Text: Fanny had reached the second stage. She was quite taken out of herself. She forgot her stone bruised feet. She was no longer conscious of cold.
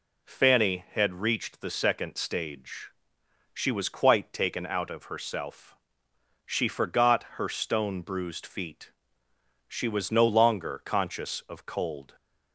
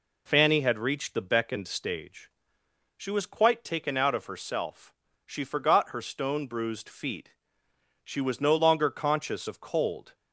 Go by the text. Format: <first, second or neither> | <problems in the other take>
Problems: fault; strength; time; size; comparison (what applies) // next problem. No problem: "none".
first | says "beckoned" for "second"; at 1.2 s